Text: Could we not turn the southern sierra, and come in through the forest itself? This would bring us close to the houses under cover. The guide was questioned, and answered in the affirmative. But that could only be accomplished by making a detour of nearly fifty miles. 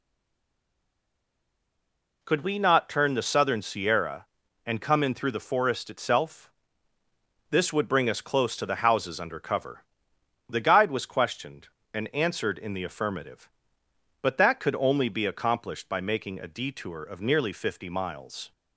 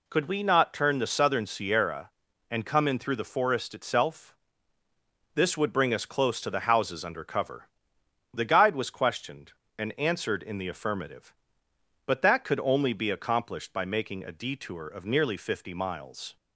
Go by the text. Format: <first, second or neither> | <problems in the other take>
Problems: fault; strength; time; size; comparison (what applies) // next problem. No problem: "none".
second | stays silent before the first word; until 2.2 s; 2.2 s long